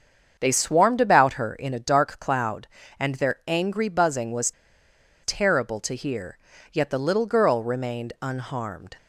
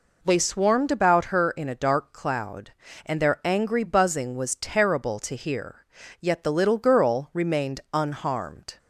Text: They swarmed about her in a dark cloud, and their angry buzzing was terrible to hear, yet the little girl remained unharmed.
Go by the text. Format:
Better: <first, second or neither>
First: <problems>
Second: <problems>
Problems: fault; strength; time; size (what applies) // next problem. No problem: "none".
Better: second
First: starts louder than the rest; strong; until 1.4 s; 7 dB // pauses between "was" and "terrible"; noticeable; at 4.5 s; 0.71 s long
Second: none